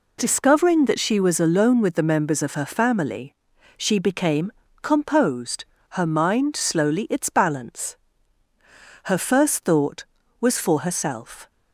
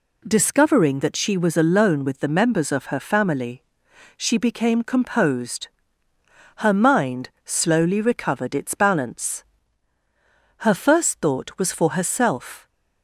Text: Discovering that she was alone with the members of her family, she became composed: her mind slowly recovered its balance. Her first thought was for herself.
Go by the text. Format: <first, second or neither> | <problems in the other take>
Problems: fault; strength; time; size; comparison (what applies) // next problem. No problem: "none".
second | pauses between "became" and "composed"; slight; at 4.5 s; 0.30 s long // skips "recovered"; at 7.0 s